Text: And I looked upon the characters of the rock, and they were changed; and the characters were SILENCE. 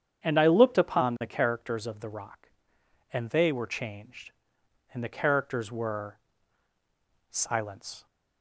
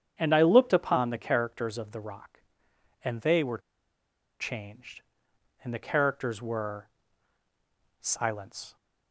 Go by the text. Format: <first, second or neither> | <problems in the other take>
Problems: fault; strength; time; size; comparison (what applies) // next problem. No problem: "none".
first | starts louder than the rest; strong; until 1.1 s; 8.5 dB; strong in the first // pauses between "were" and "changed"; noticeable; at 3.5 s; 0.81 s long // pauses between "were" and "SILENCE"; at 6.8 s; 1.1 s long; also in the first